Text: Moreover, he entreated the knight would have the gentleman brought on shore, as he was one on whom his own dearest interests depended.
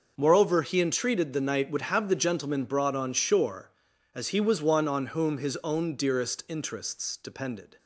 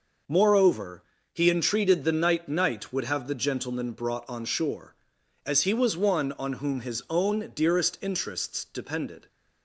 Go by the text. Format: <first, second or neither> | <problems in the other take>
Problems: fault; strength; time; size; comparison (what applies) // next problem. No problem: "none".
first | says "knight" twice; at 2.4 s